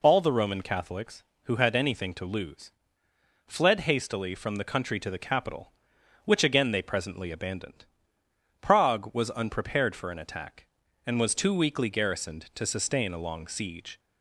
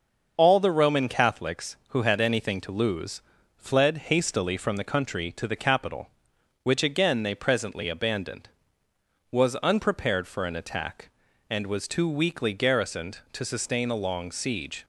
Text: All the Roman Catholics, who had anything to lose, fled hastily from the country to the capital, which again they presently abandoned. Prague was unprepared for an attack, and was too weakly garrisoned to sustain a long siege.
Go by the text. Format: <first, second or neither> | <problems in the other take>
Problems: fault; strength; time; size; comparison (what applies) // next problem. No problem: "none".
first | starts louder than the rest; until 1.3 s; 6.5 dB // skips "Prague"; at 8.8 s